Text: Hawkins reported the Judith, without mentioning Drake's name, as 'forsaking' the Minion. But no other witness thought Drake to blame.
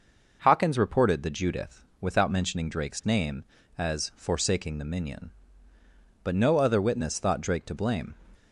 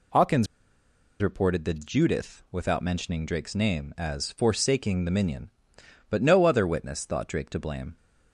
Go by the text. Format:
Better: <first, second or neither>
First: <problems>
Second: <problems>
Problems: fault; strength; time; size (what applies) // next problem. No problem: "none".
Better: first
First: none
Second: pauses between "Hawkins" and "reported"; noticeable; at 0.4 s; 0.75 s long